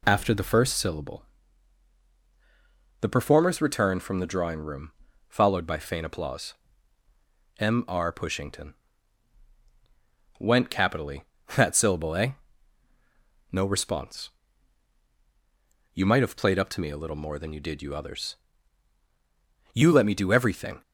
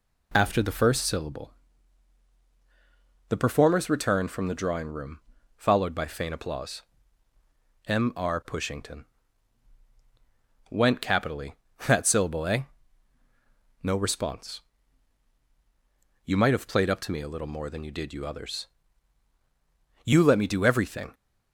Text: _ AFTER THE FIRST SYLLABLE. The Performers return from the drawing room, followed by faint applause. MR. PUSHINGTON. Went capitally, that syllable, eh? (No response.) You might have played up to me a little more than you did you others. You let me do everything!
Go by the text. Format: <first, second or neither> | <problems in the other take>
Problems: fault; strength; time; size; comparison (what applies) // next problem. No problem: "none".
neither | none